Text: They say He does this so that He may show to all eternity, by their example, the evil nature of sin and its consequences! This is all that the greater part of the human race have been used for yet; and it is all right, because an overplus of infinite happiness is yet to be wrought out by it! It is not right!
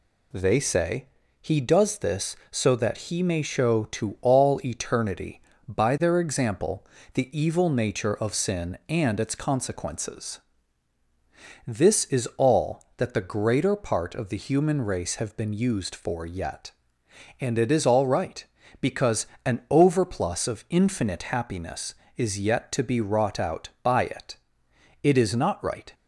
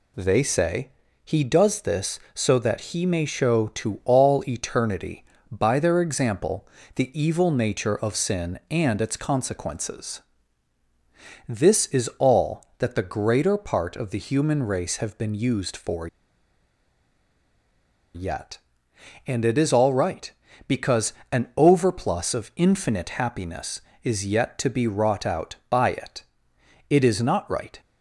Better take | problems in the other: first | pauses between "say" and "He"; slight; at 0.8 s; 0.34 s long; slight in the first // pauses between "for" and "yet"; strong; at 16.0 s; 2.0 s long // pauses between "because" and "an"; slight; at 21.1 s; 0.18 s long; slight in the first

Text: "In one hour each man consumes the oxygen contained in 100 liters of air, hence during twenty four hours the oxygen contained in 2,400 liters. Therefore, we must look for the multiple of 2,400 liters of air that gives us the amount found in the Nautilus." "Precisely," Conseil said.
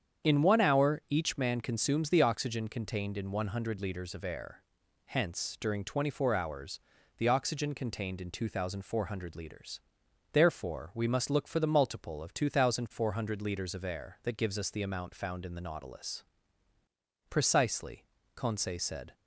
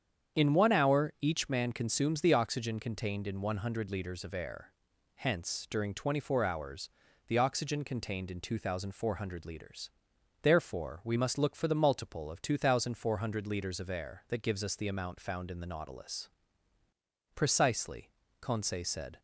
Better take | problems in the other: neither | starts louder than the rest; strong; the same in both // pauses between "hours" and "the"; the same in both

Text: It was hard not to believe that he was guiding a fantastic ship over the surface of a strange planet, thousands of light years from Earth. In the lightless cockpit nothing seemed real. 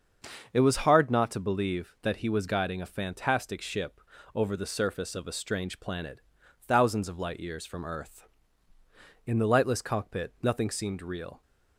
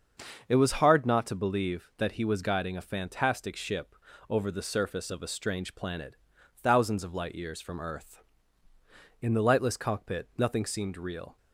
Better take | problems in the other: neither | starts louder than the rest; the same in both // pauses between "ship" and "over"; slight; the same in both

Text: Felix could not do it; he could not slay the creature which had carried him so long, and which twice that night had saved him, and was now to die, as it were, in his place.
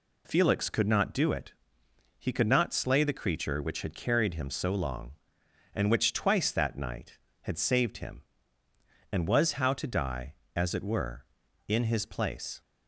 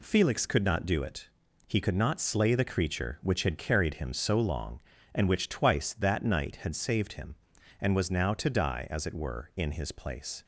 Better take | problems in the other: second | says "how" for "now"; at 9.5 s

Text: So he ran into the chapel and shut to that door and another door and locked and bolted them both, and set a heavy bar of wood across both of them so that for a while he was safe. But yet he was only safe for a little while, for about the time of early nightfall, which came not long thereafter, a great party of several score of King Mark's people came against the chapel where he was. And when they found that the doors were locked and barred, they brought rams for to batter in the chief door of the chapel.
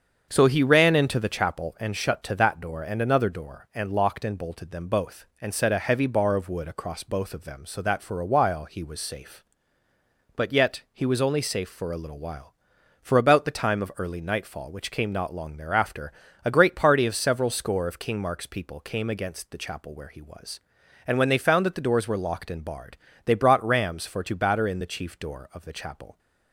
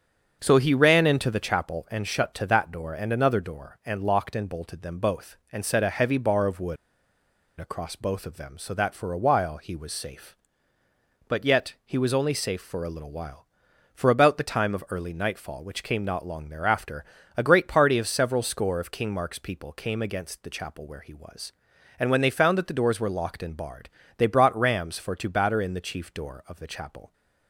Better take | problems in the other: first | starts louder than the rest; until 1.4 s; 7 dB; also in the first // pauses between "wood" and "across"; noticeable; at 6.7 s; 0.84 s long

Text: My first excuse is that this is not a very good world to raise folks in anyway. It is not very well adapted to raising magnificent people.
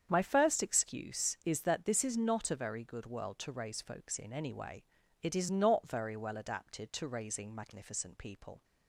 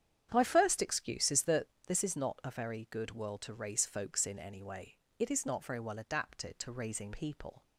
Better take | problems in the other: first | starts louder than the rest; strong; until 1.3 s; 9 dB; strong in the first // pauses between "that" and "this"; slight; at 1.6 s; 0.20 s long // skips "magnificent"; at 7.1 s

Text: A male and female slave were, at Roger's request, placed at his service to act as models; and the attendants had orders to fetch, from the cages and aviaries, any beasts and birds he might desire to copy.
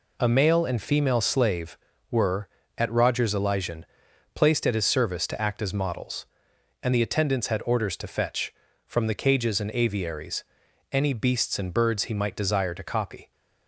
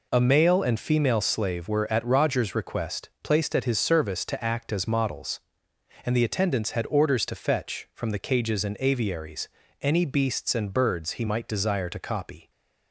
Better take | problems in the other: second | says "elysian" for "request"; at 3.3 s

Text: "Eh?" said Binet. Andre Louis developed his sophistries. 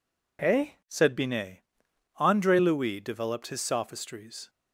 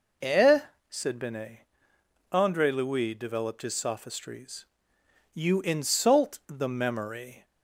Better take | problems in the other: first | goes on to say "You insult the memory"; strong; from 5.3 s on; 2.1 s long

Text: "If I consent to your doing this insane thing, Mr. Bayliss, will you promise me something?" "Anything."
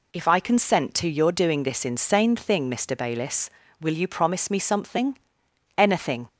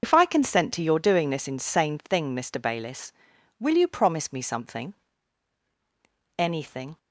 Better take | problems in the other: first | loses the start of "If"; at 0.0 s; 55 ms // starts louder than the rest; noticeable; until 1.0 s; 6 dB

